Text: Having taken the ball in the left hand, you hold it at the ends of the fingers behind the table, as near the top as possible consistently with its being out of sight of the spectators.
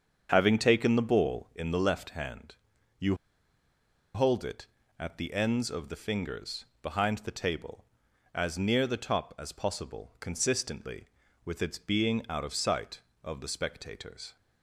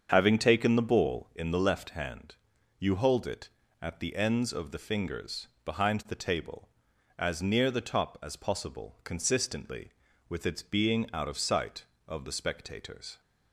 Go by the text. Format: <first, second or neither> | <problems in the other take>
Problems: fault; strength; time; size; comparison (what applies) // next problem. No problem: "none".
second | starts louder than the rest; until 1.3 s; 6.5 dB; also in the second // pauses between "you" and "hold"; at 3.1 s; 0.98 s long // pauses between "fingers" and "behind"; slight; at 6.6 s; 0.18 s long; slight in the second